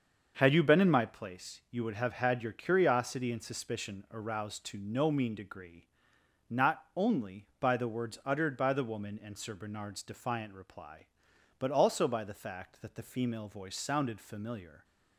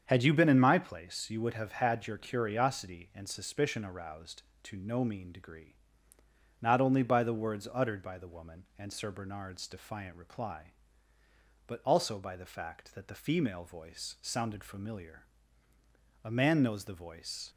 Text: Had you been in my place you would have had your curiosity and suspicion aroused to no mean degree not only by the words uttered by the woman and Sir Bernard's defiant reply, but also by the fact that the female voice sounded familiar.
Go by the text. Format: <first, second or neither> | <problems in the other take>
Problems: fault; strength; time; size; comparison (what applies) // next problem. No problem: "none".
first | starts louder than the rest; strong; until 1.0 s; 7.5 dB; also in the first // pauses between "degree" and "not"; noticeable; at 5.7 s; 0.84 s long; noticeable in the first // goes on to say "A man knows the voice"; noticeable; from 16.2 s on; 1.2 s long